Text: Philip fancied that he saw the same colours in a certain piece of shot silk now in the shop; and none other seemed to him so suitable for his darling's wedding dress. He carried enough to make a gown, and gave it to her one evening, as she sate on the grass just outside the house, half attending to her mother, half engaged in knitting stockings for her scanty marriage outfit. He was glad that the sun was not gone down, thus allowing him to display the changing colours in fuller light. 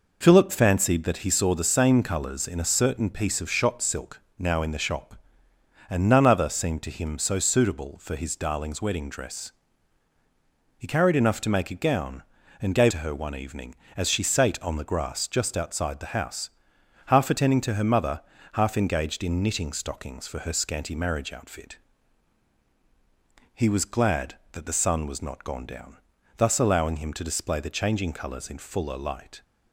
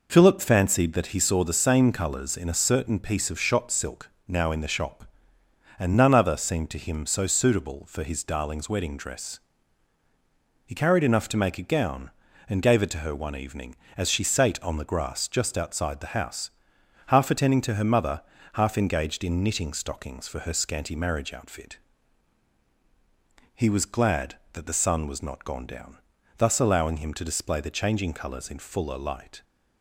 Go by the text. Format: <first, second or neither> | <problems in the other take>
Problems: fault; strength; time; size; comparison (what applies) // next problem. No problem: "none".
second | pauses between "silk" and "now"; slight; at 4.2 s; 0.16 s long; slight in the second // skips "it"; at 12.9 s